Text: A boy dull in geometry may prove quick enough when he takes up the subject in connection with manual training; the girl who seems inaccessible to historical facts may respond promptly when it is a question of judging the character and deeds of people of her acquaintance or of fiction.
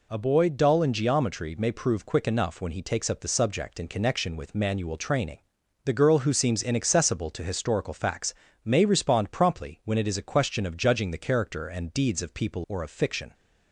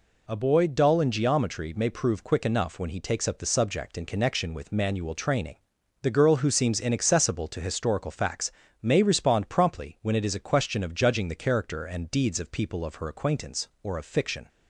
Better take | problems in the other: second | pauses between "facts" and "may"; slight; at 8.3 s; 0.28 s long; slight in the second // skips "of her acquaintance"; at 12.6 s

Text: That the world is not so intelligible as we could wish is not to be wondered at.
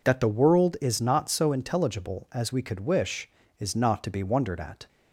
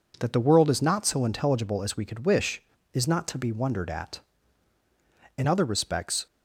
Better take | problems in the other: first | goes on to say "In other respects"; noticeable; from 5.3 s on; 0.88 s long

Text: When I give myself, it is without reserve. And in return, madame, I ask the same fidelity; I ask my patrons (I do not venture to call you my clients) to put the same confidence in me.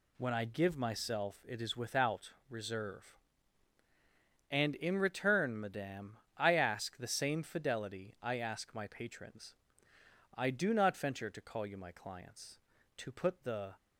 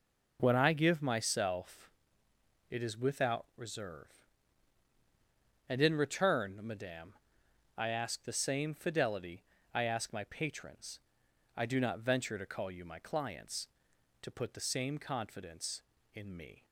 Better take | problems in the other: second | pauses between "without" and "reserve"; slight; at 2.3 s; 0.18 s long // stops before "same confidence in me"; at 13.7 s

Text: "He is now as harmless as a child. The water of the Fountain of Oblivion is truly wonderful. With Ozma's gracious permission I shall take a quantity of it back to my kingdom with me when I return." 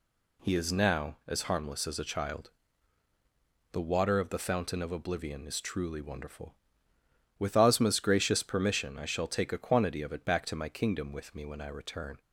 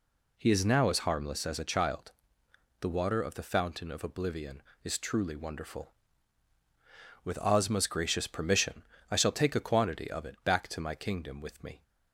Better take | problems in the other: first | pauses between "permission" and "I"; slight; at 8.8 s; 0.26 s long // stops before "when I return"; at 11.8 s

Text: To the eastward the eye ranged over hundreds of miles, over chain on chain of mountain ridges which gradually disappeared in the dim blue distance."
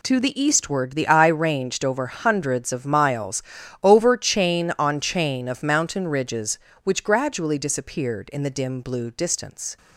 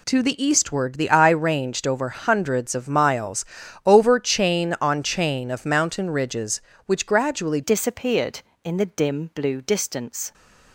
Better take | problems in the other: first | changes voice at "disappeared"; from 7.6 s on; 2.7 s long

